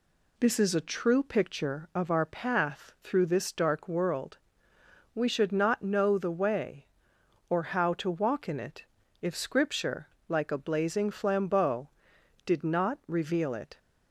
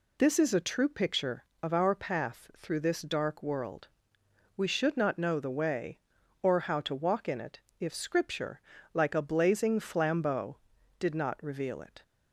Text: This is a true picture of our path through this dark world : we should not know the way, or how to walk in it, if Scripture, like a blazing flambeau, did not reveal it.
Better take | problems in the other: neither | none

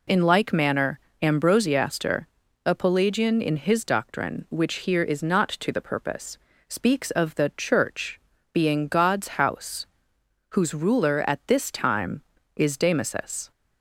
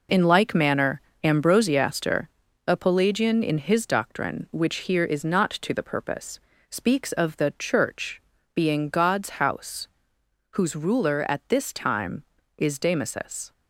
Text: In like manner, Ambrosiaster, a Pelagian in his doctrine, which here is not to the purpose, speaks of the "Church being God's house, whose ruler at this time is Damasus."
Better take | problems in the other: first | gets quieter; strong; throughout; 8 dB // pauses between "Church" and "being"; slight; at 8.2 s; 0.36 s long; slight in the first

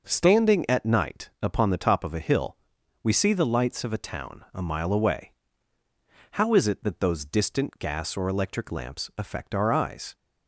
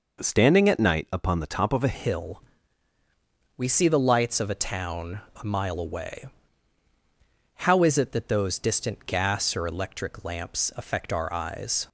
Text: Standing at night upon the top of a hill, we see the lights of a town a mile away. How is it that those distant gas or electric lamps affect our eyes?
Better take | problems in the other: first | changes voice at "hill"; from 1.9 s on; 9.9 s long // pauses between "town" and "a"; slight; at 5.2 s; 0.20 s long

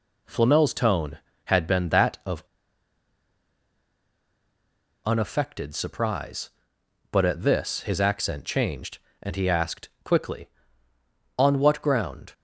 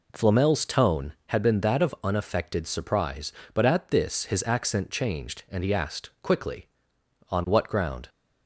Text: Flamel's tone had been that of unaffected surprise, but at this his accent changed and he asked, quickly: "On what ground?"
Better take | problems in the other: second | pauses between "of" and "unaffected"; strong; at 2.4 s; 2.6 s long

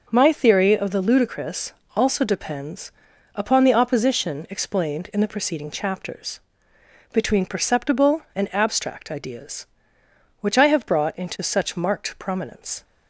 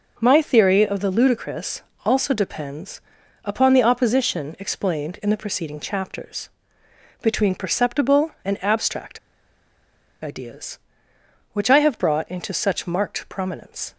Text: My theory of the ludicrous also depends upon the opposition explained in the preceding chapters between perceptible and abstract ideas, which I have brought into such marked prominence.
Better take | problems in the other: first | pauses between "ludicrous" and "also"; slight; at 1.8 s; 0.24 s long; slight in the first // pauses between "depends" and "upon"; at 3.0 s; 0.42 s long; also in the first // pauses between "chapters" and "between"; noticeable; at 6.4 s; 0.72 s long; noticeable in the first // pauses between "abstract" and "ideas"; at 9.1 s; 1.0 s long

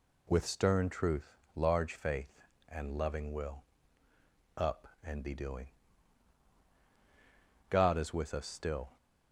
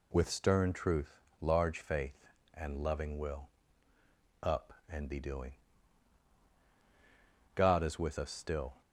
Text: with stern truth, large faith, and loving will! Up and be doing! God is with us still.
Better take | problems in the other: neither | none

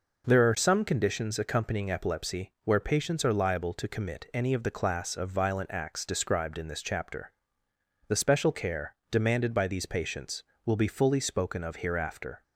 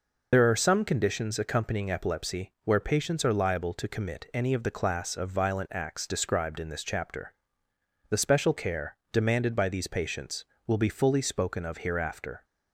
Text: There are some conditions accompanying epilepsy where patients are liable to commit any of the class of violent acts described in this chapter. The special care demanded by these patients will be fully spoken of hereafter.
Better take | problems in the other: first | loses the start of "There"; at 0.3 s; 75 ms // pauses between "care" and "demanded"; slight; at 8.9 s; 0.16 s long; slight in the first

